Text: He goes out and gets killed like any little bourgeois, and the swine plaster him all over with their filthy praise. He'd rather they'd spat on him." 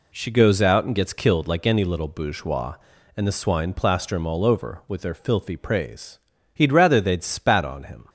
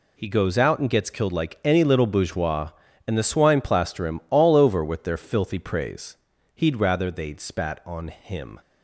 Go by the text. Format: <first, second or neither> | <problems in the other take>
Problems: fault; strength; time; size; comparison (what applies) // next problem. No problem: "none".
second | says "She" for "He"; at 0.1 s